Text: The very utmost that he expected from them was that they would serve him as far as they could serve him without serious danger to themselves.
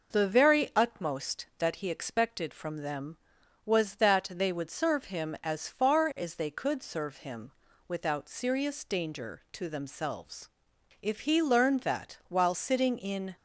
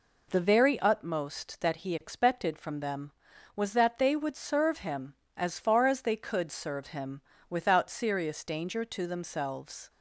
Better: second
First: pauses between "him" and "without"; slight; at 7.5 s; 0.36 s long // goes on to say "If he learned that while sitting in"; strong; from 11.0 s on; 2.3 s long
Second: pauses between "him" and "without"; slight; at 7.1 s; 0.30 s long

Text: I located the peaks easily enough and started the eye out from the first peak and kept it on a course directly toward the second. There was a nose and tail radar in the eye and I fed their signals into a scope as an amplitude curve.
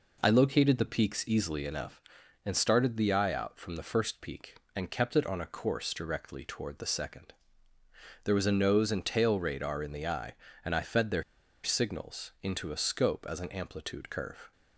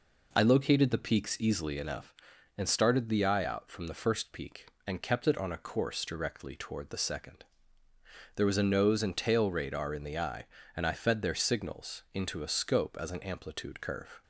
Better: second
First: pauses between "their" and "signals"; at 11.2 s; 0.40 s long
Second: none

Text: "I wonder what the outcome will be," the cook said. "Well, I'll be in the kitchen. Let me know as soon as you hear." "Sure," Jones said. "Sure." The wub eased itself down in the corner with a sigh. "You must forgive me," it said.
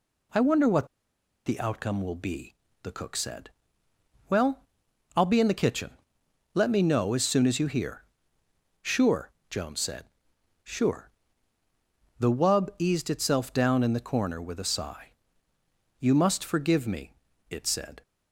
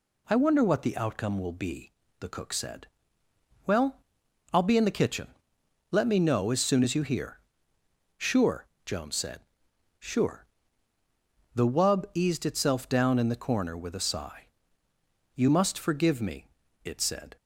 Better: second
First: pauses between "what" and "the"; noticeable; at 0.8 s; 0.58 s long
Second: none

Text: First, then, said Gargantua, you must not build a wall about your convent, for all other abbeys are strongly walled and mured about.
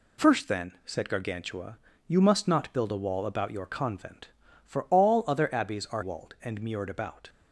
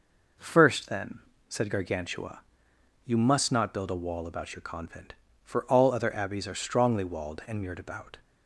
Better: second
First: skips "strongly"; at 6.0 s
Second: none

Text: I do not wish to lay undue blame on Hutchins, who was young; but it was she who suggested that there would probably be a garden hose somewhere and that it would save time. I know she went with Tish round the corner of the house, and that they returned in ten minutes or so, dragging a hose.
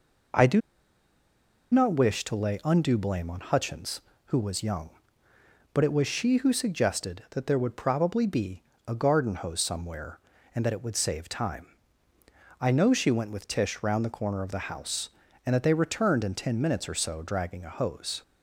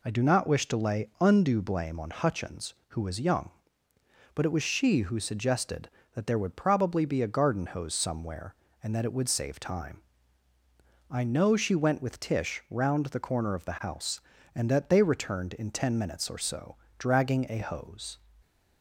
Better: second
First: pauses between "do" and "not"; at 0.6 s; 1.1 s long // pauses between "be" and "a"; slight; at 8.6 s; 0.26 s long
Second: none

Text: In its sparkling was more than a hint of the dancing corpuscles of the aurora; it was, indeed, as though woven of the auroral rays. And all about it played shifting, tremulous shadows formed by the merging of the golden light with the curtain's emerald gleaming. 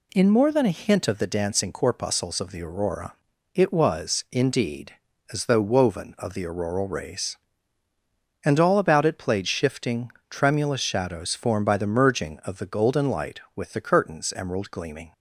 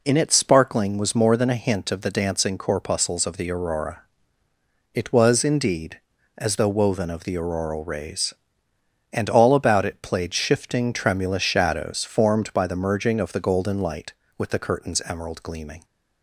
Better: second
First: skips "its sparkling was"; at 0.2 s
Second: none

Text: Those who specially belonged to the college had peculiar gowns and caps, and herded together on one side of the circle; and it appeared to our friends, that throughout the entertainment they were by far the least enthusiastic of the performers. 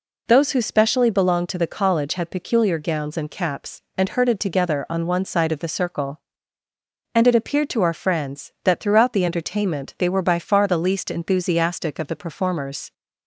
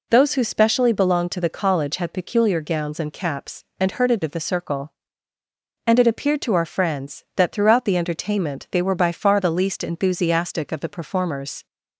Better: first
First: none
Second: skips "together on one side"; at 4.2 s

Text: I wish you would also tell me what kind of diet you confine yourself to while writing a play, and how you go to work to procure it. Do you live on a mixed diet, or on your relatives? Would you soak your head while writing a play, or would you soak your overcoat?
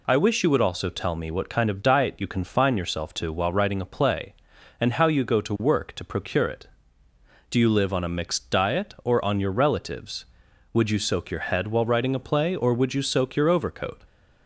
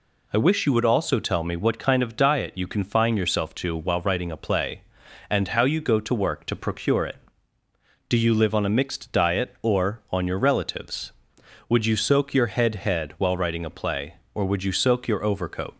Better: first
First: none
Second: says "head" twice; at 12.7 s

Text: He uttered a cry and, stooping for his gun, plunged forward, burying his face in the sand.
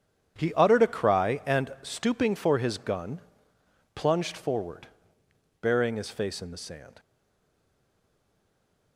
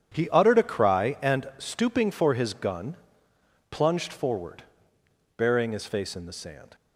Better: second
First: stays silent after the last word; noticeable; from 6.9 s on; 2.0 s long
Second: none

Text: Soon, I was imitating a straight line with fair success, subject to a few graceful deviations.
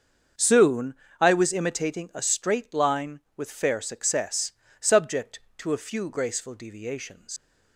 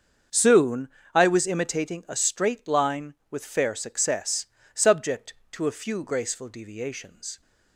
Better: second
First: starts louder than the rest; until 1.6 s; 7 dB // leaves "deviations" unfinished; at 7.3 s; 105 ms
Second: starts louder than the rest; until 1.5 s; 7 dB

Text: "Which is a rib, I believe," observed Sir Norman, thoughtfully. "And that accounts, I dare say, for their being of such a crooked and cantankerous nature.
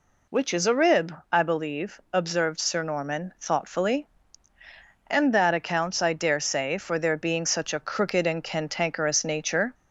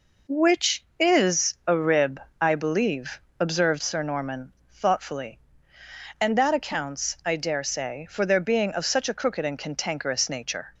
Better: second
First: skips "of"; at 7.4 s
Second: none

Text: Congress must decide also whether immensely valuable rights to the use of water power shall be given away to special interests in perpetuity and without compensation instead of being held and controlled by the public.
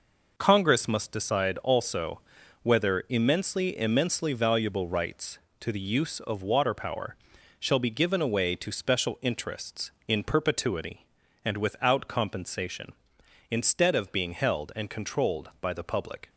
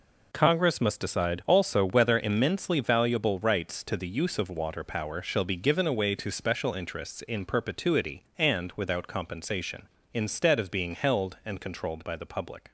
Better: second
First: pauses between "also" and "whether"; at 2.2 s; 0.40 s long // says "immensely" twice; at 3.7 s // pauses between "power" and "shall"; at 7.1 s; 0.44 s long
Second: none

